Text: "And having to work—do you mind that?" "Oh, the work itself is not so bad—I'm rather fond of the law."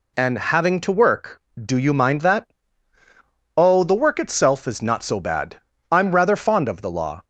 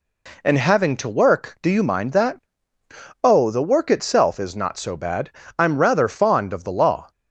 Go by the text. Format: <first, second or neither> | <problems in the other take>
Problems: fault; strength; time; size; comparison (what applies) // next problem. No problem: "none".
neither | none